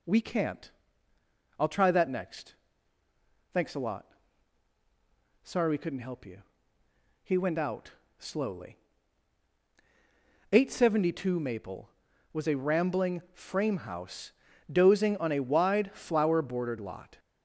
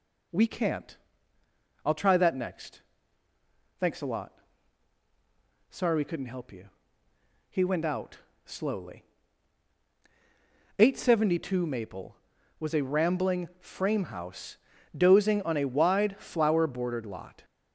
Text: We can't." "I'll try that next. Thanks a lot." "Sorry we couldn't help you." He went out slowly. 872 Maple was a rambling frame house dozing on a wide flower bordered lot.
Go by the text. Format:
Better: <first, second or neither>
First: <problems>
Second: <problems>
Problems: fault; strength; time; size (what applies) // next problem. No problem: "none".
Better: neither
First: pauses between "out" and "slowly"; slight; at 7.9 s; 0.26 s long // pauses between "house" and "dozing"; at 14.3 s; 0.40 s long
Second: pauses between "out" and "slowly"; slight; at 8.1 s; 0.26 s long // pauses between "house" and "dozing"; at 14.5 s; 0.40 s long